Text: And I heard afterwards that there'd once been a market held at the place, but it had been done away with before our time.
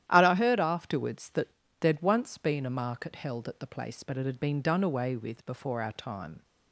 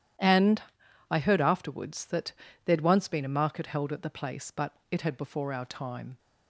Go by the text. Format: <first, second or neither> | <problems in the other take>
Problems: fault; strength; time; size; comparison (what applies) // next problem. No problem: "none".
first | starts louder than the rest; strong; until 1.6 s; 11 dB; strong in the first // pauses between "And" and "I"; noticeable; at 0.6 s; 0.48 s long // pauses between "that" and "there'd"; slight; at 2.3 s; 0.32 s long; slight in the first // pauses between "but" and "it"; slight; at 4.7 s; 0.16 s long // skips "been done away with"; at 5.1 s